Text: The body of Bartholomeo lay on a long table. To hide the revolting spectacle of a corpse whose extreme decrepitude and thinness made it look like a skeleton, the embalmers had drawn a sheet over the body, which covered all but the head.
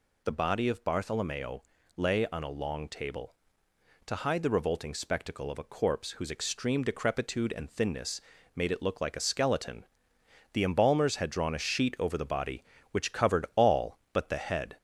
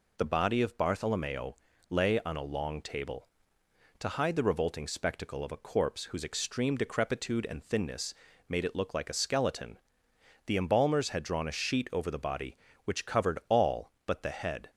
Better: second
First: gets louder; slight; throughout; 2.5 dB // pauses between "Bartholomeo" and "lay"; slight; at 1.6 s; 0.34 s long // pauses between "thinness" and "made"; slight; at 8.2 s; 0.34 s long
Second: pauses between "Bartholomeo" and "lay"; slight; at 1.5 s; 0.34 s long // pauses between "thinness" and "made"; slight; at 8.1 s; 0.34 s long

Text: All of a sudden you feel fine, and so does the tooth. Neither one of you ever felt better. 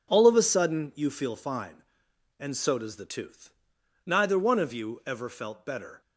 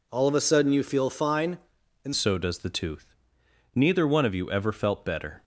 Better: first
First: none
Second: changes voice at "so"; from 2.1 s on; 3.3 s long

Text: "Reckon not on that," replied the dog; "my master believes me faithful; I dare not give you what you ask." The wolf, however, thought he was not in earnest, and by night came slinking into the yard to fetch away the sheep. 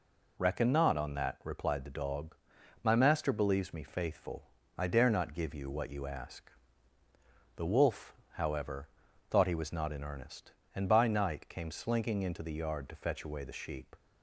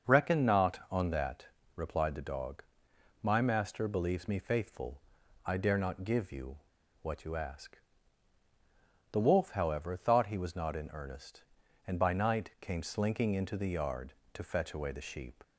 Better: first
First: none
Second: starts louder than the rest; until 1.1 s; 6.5 dB // pauses between "you" and "what"; at 6.5 s; 0.44 s long

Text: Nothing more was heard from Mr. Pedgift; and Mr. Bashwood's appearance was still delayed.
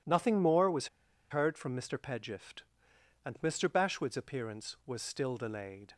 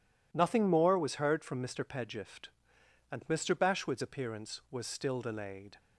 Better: second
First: pauses between "was" and "heard"; at 0.8 s; 0.43 s long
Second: none

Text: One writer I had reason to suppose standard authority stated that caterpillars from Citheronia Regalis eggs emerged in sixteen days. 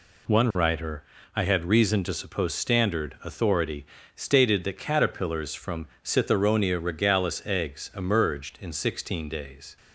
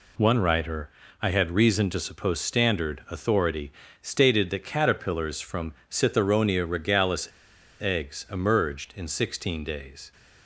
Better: first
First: pauses between "writer" and "I"; slight; at 1.0 s; 0.32 s long // pauses between "authority" and "stated"; slight; at 3.8 s; 0.30 s long // pauses between "from" and "Citheronia"; slight; at 5.8 s; 0.16 s long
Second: pauses between "writer" and "I"; slight; at 0.8 s; 0.32 s long // pauses between "authority" and "stated"; slight; at 3.7 s; 0.30 s long // pauses between "from" and "Citheronia"; slight; at 5.7 s; 0.16 s long // pauses between "Regalis" and "eggs"; noticeable; at 7.2 s; 0.51 s long

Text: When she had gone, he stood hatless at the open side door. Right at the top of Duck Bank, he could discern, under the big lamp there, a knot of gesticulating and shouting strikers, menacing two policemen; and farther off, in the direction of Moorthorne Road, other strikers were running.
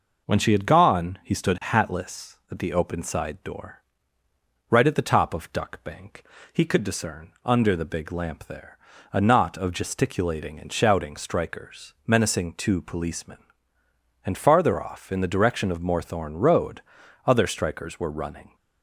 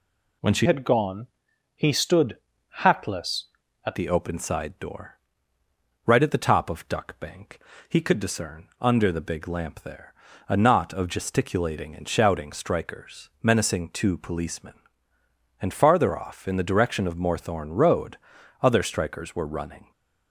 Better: first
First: none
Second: changes voice from "had" to "at"; from 0.6 to 3.9 s; 3.3 s long // pauses between "stood" and "hatless"; noticeable; at 2.3 s; 0.46 s long

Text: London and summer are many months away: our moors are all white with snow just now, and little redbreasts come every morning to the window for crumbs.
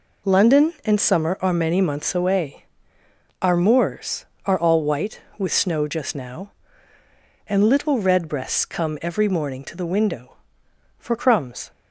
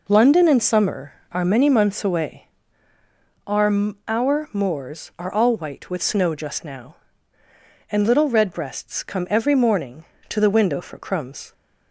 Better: first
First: none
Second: says "our" twice; at 4.0 s

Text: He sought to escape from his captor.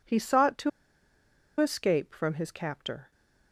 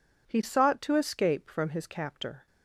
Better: second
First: pauses between "to" and "escape"; noticeable; at 0.6 s; 0.90 s long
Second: none

